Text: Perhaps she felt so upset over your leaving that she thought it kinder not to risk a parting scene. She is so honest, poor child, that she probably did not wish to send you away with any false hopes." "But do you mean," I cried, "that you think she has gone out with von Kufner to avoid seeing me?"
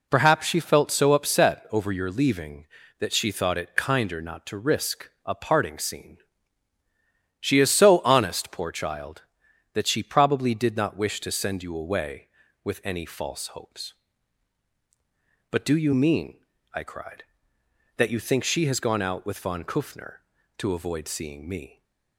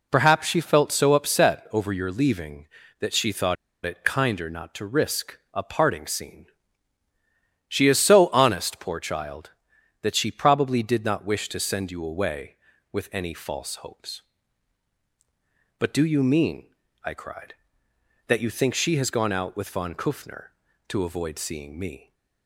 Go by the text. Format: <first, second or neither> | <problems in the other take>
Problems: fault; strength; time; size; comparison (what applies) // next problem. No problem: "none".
first | pauses between "thought" and "it"; slight; at 3.5 s; 0.30 s long